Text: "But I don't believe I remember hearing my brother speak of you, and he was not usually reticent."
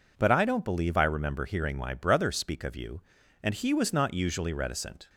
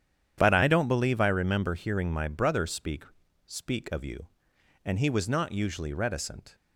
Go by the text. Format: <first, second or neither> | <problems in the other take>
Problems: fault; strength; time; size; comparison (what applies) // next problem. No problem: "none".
first | starts louder than the rest; strong; until 1.3 s; 9.5 dB // says "speak" twice; at 3.4 s